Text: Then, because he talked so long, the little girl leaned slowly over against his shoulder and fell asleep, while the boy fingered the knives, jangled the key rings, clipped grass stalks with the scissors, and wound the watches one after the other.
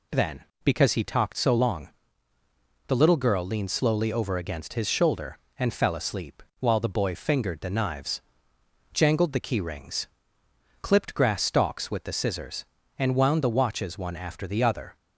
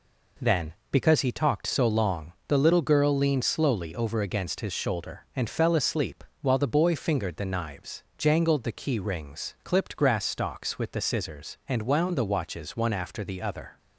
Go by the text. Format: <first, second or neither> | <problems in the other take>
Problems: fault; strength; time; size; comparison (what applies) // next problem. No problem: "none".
neither | none